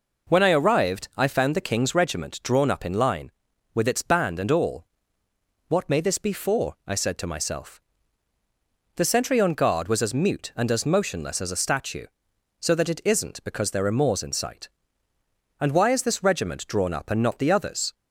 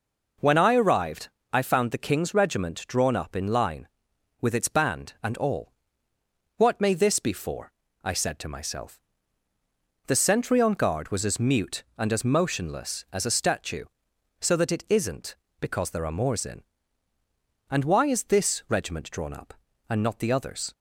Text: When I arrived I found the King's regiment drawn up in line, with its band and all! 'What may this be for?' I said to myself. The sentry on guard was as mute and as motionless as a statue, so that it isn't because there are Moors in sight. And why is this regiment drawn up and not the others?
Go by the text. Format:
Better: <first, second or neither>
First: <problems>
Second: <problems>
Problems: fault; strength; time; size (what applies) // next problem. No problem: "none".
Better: first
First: none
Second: pauses between "arrived" and "I"; slight; at 1.2 s; 0.24 s long // skips "sight"; at 17.1 s